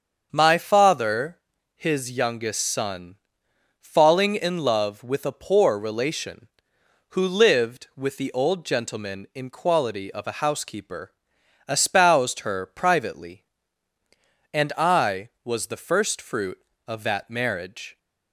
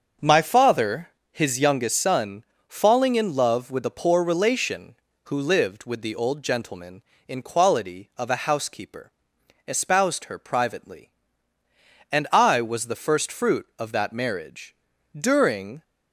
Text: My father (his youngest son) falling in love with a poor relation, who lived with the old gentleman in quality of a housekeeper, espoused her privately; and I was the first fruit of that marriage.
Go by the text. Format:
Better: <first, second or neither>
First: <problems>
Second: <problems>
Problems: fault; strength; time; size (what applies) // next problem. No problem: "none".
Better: first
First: starts louder than the rest; until 1.3 s; 7 dB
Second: starts louder than the rest; until 1.4 s; 7 dB // goes on to say "During"; noticeable; from 15.1 s on; 0.66 s long